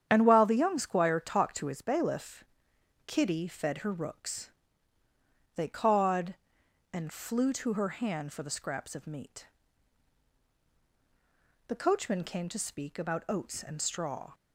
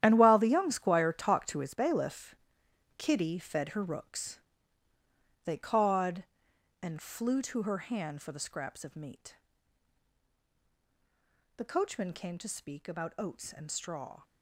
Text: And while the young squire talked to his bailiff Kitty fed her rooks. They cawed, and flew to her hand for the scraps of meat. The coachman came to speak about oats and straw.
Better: first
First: starts louder than the rest; strong; until 1.1 s; 9 dB // pauses between "bailiff" and "Kitty"; noticeable; at 2.4 s; 0.62 s long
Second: gets quieter; strong; throughout; 12.5 dB // starts louder than the rest; strong; until 1.0 s; 11 dB // pauses between "bailiff" and "Kitty"; noticeable; at 2.3 s; 0.62 s long

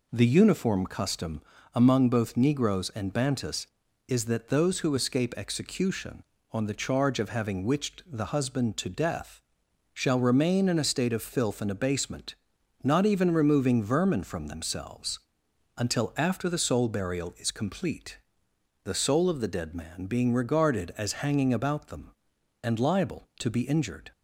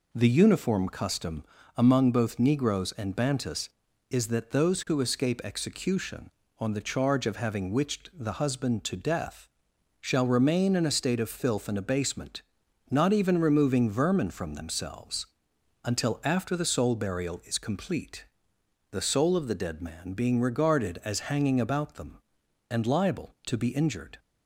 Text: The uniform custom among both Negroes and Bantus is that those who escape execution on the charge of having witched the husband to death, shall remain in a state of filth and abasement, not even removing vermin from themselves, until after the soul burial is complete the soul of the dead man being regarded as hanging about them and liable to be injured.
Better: neither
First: pauses between "custom" and "among"; slight; at 1.4 s; 0.34 s long // pauses between "complete" and "the"; noticeable; at 18.1 s; 0.64 s long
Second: pauses between "custom" and "among"; slight; at 1.4 s; 0.34 s long // pauses between "complete" and "the"; noticeable; at 18.2 s; 0.64 s long

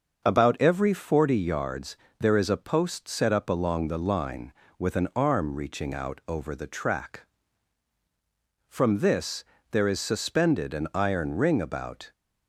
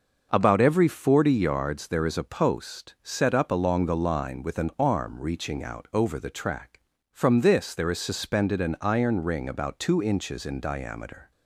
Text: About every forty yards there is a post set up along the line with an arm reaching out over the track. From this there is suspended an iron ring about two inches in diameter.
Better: second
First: starts louder than the rest; until 1.3 s; 6.5 dB // pauses between "yards" and "there"; slight; at 1.9 s; 0.24 s long // pauses between "this" and "there"; slight; at 9.4 s; 0.28 s long // stops before "two inches in diameter"; at 12.1 s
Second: starts louder than the rest; noticeable; until 1.3 s; 6 dB

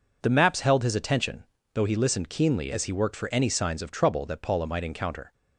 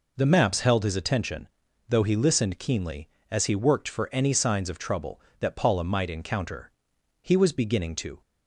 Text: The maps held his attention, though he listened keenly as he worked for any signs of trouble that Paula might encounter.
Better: first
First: none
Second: goes on to say "He was beginning to"; noticeable; from 7.2 s on; 1.0 s long

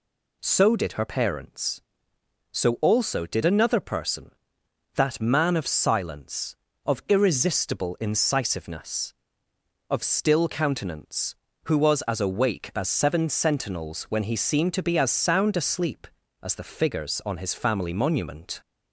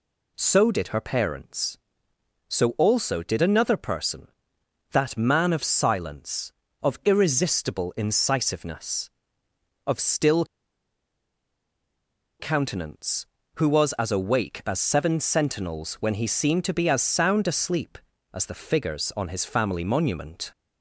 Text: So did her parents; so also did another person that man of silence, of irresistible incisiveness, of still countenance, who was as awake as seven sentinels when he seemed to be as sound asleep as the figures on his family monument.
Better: first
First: none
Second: pauses between "still" and "countenance"; strong; at 10.4 s; 1.9 s long

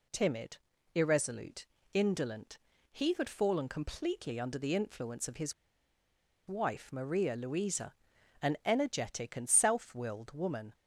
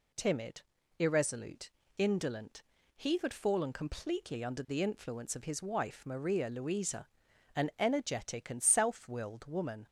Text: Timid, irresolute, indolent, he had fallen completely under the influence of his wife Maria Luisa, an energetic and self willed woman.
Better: second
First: pauses between "his" and "wife"; noticeable; at 5.5 s; 0.94 s long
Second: none

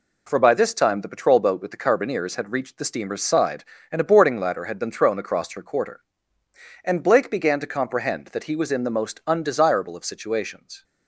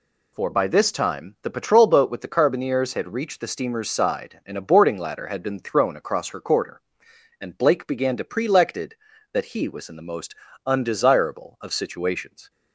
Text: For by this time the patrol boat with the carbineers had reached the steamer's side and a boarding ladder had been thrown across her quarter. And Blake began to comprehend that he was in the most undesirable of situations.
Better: first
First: none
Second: says "prelected" for "comprehend"; at 8.2 s // pauses between "most" and "undesirable"; slight; at 10.3 s; 0.32 s long

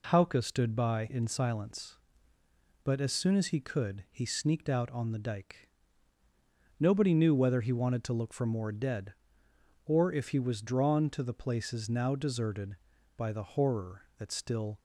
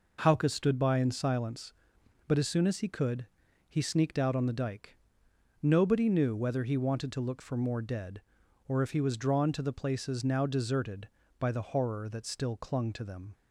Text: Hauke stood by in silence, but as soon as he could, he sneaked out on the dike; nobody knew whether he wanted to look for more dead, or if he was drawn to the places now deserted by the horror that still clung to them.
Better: second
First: stops before "clung to them"; at 14.7 s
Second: none

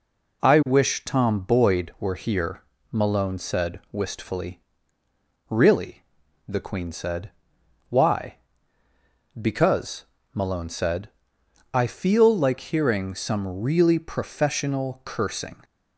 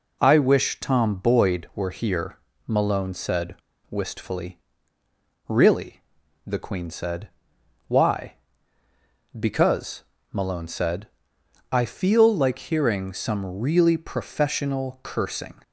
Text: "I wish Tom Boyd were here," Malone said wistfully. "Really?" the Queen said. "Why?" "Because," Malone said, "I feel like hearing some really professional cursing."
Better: first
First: none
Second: pauses between "said" and "wistfully"; at 3.5 s; 0.37 s long

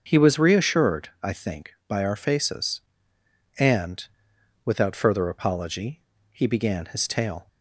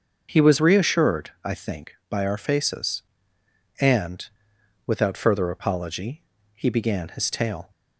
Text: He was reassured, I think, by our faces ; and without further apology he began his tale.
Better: neither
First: starts louder than the rest; until 1.0 s; 6.5 dB // pauses between "and" and "without"; noticeable; at 4.0 s; 0.62 s long // pauses between "apology" and "he"; slight; at 5.9 s; 0.32 s long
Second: starts louder than the rest; until 1.3 s; 6.5 dB // pauses between "and" and "without"; noticeable; at 4.2 s; 0.62 s long // pauses between "apology" and "he"; slight; at 6.2 s; 0.34 s long

